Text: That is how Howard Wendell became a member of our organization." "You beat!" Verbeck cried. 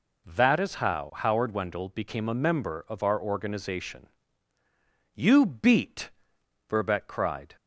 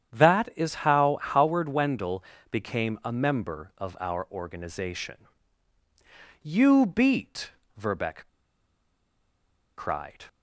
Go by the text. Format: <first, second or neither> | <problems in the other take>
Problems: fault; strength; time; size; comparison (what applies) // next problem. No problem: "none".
first | starts louder than the rest; strong; until 1.2 s; 8.5 dB // pauses between "Wendell" and "became"; slight; at 2.2 s; 0.28 s long // pauses between "Verbeck" and "cried"; strong; at 8.2 s; 1.4 s long